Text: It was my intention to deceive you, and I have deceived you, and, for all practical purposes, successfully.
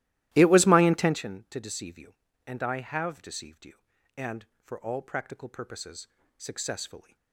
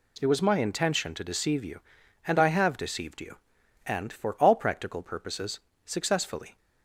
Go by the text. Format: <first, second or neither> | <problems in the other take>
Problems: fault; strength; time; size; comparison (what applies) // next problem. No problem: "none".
second | starts louder than the rest; strong; until 1.2 s; 15 dB